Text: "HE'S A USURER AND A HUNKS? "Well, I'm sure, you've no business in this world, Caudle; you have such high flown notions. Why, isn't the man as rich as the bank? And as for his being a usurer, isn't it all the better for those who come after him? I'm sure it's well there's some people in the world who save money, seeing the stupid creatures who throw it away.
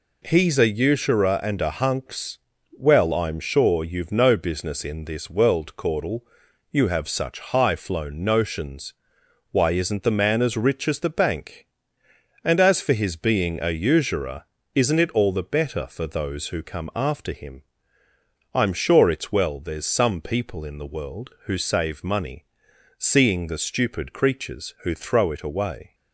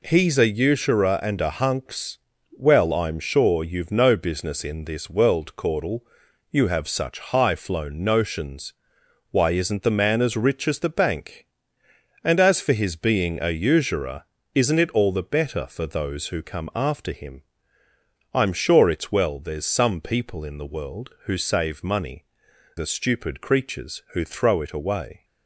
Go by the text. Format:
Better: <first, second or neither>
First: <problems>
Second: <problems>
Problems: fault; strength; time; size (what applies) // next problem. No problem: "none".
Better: first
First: none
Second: skips "seeing"; at 22.5 s